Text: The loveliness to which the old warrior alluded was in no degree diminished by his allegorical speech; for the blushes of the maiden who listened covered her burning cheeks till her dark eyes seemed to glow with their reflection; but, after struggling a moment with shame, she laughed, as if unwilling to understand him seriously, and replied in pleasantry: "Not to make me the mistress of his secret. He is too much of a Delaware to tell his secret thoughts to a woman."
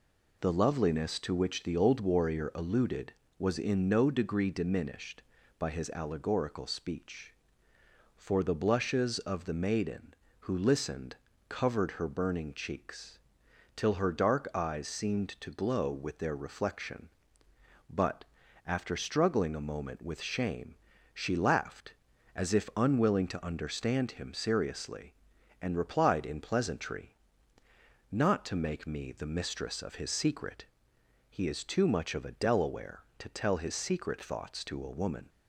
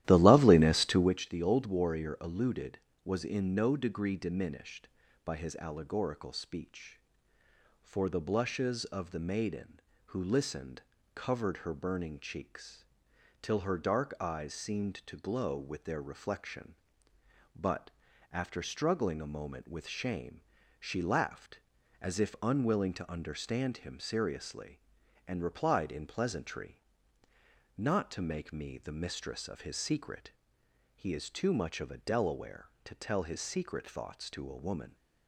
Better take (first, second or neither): first